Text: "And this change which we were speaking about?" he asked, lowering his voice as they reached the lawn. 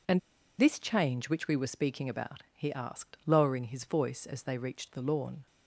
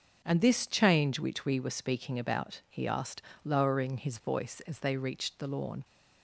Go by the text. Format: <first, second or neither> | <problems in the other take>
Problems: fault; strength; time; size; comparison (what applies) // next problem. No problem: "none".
second | pauses between "And" and "this"; at 0.1 s; 0.39 s long